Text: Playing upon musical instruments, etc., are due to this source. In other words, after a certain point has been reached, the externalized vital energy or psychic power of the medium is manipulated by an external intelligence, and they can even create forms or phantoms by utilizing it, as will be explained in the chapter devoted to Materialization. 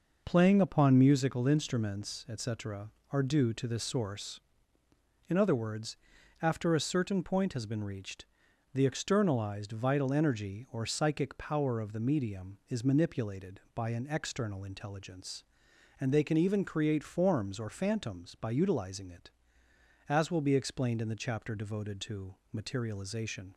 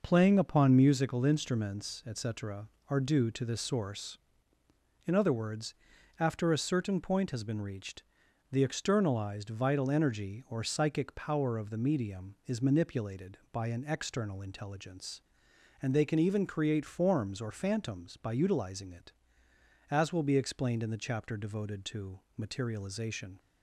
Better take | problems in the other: neither | pauses between "to" and "Materialization"; slight; the same in both

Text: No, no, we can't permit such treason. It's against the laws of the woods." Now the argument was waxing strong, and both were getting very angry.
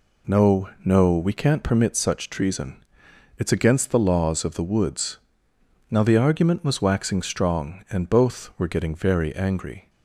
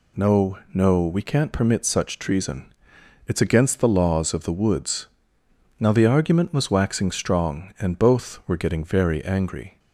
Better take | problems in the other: second | starts louder than the rest; slight; until 2.0 s; 3 dB

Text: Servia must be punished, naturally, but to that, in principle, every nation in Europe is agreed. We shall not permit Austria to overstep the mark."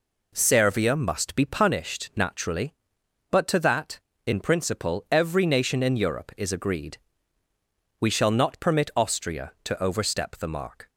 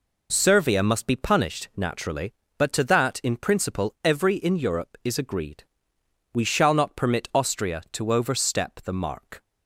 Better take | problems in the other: first | skips "nation"; at 4.3 s

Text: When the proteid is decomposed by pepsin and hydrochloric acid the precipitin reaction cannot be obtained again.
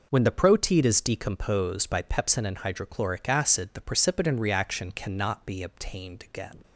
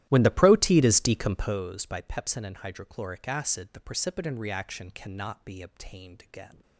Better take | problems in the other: first | starts louder than the rest; strong; until 1.6 s; 14 dB

